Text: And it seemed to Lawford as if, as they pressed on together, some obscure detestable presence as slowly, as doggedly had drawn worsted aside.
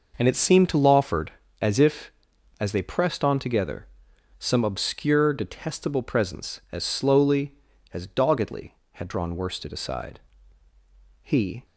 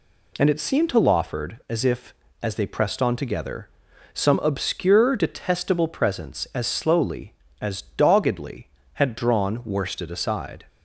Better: second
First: goes on to say "He"; slight; from 11.2 s on; 0.44 s long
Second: none

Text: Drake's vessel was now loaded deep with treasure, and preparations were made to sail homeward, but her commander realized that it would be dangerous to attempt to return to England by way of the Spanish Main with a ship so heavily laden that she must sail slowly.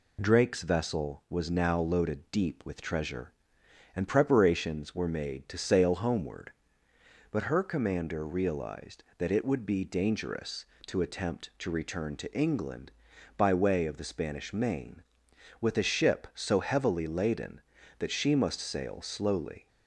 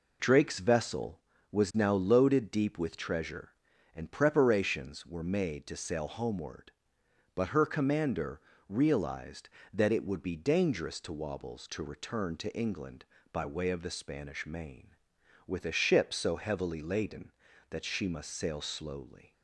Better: first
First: none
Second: pauses between "commander" and "realized"; slight; at 8.4 s; 0.26 s long // says "wobbles" for "attempt"; at 11.1 s

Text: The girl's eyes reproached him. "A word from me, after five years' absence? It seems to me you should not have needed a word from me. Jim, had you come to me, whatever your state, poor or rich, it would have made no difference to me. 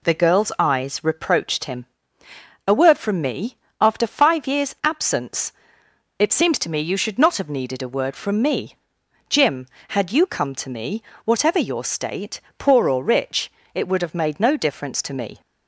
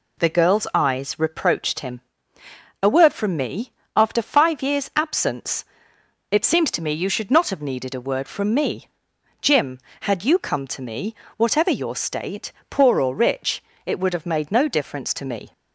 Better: neither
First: none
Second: none

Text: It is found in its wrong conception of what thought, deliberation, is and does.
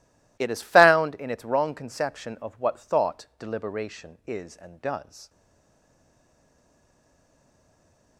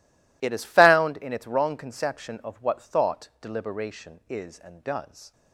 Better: second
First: stays silent after the last word; strong; from 5.2 s on; 2.9 s long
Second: none

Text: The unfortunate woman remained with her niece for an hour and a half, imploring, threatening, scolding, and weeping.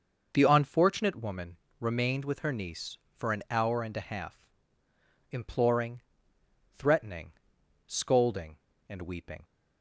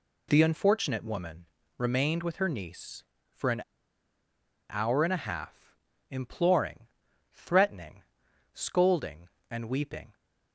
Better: first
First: pauses between "woman" and "remained"; slight; at 1.5 s; 0.22 s long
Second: pauses between "woman" and "remained"; slight; at 1.4 s; 0.32 s long // pauses between "an" and "hour"; at 3.6 s; 1.0 s long

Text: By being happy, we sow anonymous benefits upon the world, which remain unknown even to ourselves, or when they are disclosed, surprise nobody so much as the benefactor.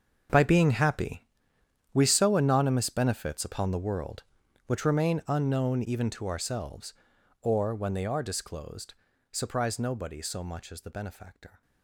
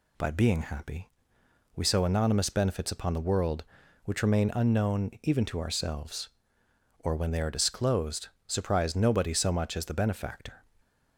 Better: second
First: gets quieter; strong; throughout; 16 dB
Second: none

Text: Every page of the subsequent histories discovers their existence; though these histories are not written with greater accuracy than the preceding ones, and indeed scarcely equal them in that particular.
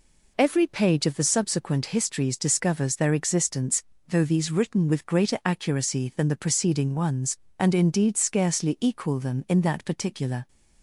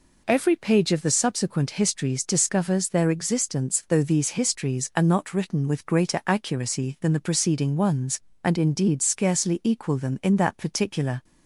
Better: second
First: skips "histories are not"; at 4.4 s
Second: none

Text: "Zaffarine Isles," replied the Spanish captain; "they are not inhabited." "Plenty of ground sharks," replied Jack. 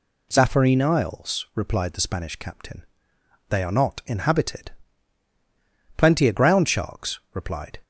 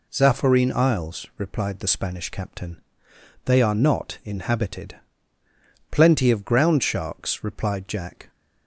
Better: second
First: stops before "Jack"; at 7.8 s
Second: none

